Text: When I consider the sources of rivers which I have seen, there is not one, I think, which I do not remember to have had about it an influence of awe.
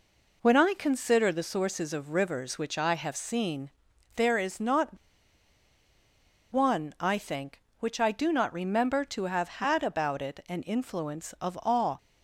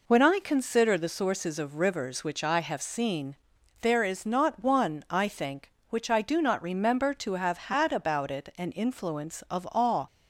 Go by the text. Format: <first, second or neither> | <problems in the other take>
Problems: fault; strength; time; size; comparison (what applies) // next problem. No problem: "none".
second | pauses between "not" and "one"; strong; at 4.9 s; 1.5 s long